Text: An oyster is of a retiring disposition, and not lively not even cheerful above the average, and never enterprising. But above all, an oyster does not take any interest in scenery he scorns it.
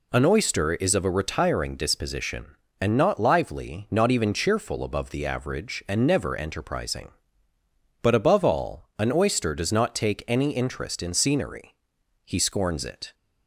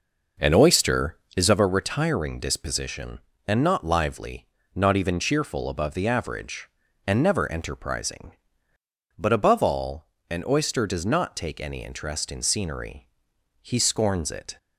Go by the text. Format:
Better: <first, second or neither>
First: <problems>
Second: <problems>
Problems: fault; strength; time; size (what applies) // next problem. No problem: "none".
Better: first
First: pauses between "scenery" and "he"; noticeable; at 11.7 s; 0.50 s long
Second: starts louder than the rest; noticeable; until 1.6 s; 5 dB // pauses between "lively" and "not"; slight; at 4.4 s; 0.30 s long // pauses between "scenery" and "he"; noticeable; at 13.0 s; 0.56 s long